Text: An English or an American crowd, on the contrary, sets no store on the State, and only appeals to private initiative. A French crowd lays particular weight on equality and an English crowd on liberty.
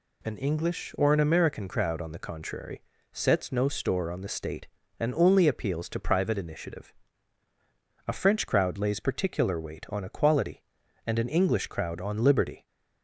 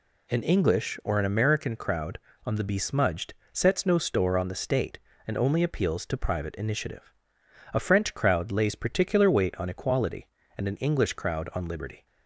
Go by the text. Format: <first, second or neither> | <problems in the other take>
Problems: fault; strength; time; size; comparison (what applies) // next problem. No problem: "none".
first | says "besmudged" for "contrary"; at 2.6 s